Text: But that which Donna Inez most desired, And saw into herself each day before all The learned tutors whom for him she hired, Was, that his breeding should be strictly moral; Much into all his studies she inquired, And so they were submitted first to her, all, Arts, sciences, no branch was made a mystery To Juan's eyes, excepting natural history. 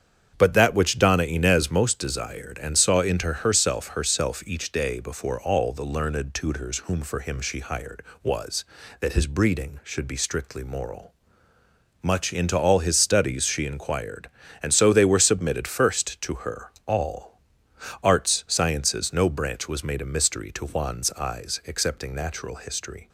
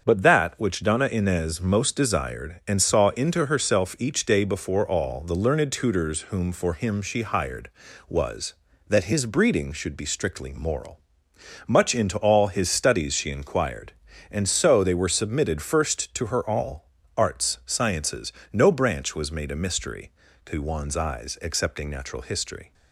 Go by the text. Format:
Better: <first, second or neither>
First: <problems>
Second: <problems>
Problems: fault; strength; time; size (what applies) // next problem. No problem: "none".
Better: second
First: starts louder than the rest; strong; until 1.3 s; 8 dB // says "herself" twice; at 3.8 s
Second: starts louder than the rest; until 1.0 s; 7 dB